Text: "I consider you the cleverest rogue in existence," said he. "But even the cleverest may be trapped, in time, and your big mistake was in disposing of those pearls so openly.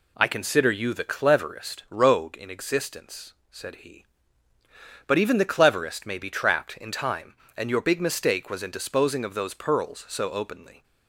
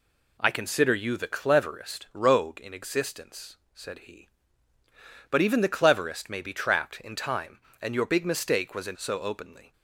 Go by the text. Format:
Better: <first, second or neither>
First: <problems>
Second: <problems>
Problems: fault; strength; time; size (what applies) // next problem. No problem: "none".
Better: first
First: none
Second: skips "disposing of those pearls"; at 8.9 s